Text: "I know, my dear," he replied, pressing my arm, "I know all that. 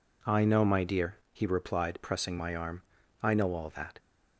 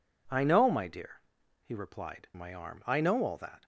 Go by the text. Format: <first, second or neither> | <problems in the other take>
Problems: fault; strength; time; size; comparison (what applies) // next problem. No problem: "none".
first | skips "pressing"; at 2.3 s